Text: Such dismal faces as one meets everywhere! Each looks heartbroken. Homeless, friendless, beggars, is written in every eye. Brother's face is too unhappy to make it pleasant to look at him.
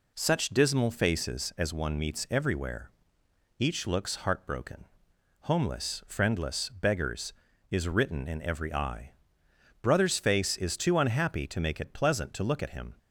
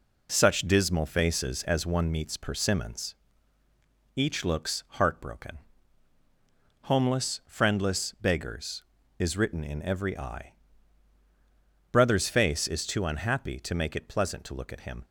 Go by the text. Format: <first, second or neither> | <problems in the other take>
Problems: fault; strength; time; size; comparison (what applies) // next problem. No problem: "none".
first | says "persimmons" for "everywhere"; at 2.3 s